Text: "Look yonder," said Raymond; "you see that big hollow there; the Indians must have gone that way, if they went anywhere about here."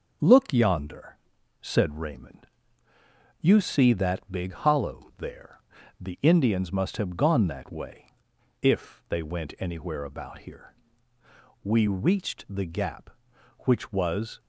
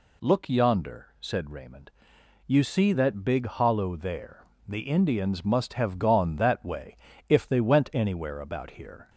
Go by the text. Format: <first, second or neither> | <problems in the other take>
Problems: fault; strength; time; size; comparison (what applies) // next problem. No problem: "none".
second | starts louder than the rest; until 1.6 s; 6.5 dB // goes on to say "We reached the gap which was"; strong; from 11.6 s on; 2.7 s long